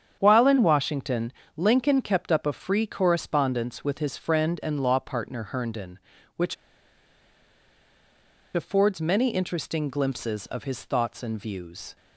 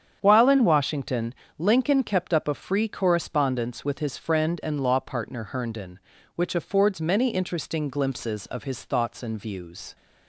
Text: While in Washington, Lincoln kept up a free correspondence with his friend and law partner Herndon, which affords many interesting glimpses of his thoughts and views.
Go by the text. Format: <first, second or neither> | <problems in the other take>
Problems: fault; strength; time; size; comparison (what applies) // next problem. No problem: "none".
second | starts louder than the rest; strong; until 1.2 s; 8.5 dB; strong in the second // pauses between "which" and "affords"; strong; at 6.5 s; 2.0 s long